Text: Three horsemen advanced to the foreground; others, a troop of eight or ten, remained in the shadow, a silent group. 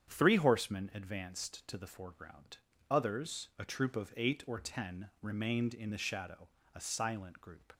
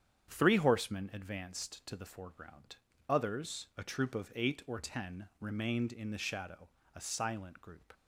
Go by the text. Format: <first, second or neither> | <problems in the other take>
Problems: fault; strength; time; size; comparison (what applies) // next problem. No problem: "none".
neither | starts louder than the rest; strong; the same in both